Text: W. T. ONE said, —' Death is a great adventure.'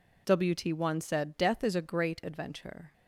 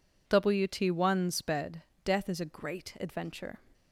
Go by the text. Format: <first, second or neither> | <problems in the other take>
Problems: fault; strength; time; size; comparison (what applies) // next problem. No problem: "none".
first | says "sped" for "said"; at 1.2 s